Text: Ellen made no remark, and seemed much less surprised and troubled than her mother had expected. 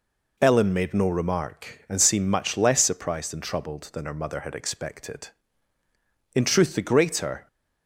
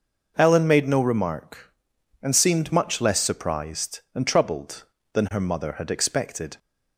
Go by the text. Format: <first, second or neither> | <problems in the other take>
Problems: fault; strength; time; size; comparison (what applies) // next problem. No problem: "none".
second | goes on to say "In truth the greater"; noticeable; from 6.3 s on; 1.1 s long